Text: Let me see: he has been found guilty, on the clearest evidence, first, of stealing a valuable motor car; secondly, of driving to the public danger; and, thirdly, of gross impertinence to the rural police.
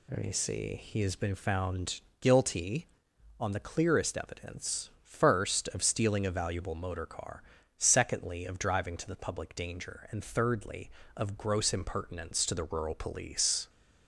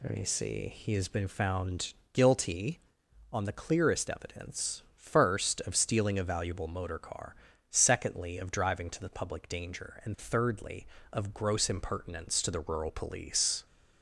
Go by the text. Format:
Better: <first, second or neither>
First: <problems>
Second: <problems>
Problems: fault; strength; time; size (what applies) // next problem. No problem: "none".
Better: neither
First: pauses between "found" and "guilty"; slight; at 2.0 s; 0.18 s long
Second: pauses between "found" and "guilty"; slight; at 1.9 s; 0.18 s long